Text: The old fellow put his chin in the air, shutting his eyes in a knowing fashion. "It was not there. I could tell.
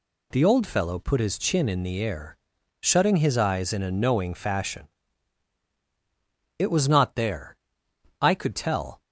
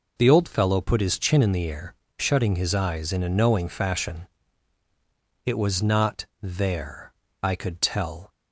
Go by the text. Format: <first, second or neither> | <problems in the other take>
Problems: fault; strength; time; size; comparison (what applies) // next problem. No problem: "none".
neither | none